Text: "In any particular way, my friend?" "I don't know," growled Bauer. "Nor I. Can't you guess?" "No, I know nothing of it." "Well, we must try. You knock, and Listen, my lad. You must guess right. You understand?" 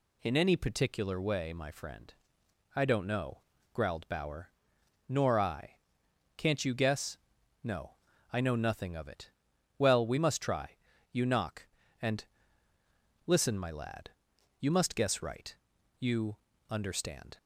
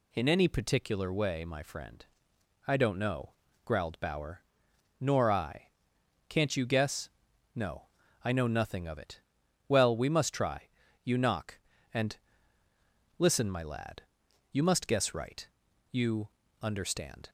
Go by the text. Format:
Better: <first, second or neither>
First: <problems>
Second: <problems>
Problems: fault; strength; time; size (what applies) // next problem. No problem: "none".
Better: neither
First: pauses between "and" and "Listen"; at 12.2 s; 1.0 s long // pauses between "You" and "understand"; slight; at 16.3 s; 0.30 s long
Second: pauses between "and" and "Listen"; at 12.1 s; 1.0 s long // pauses between "You" and "understand"; slight; at 16.2 s; 0.30 s long